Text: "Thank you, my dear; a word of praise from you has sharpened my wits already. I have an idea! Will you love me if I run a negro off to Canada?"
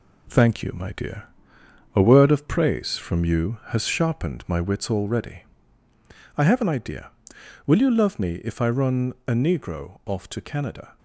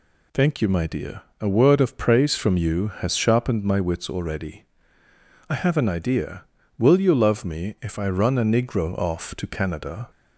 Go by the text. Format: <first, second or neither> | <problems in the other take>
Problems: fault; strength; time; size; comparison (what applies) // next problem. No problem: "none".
second | gets quieter; throughout; 7 dB